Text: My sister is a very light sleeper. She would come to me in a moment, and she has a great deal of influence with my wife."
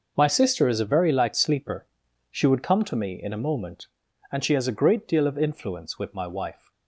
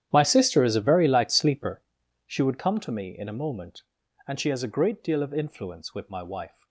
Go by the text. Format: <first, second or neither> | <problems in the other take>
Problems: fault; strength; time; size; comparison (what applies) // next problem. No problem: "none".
first | starts louder than the rest; strong; until 1.9 s; 10.5 dB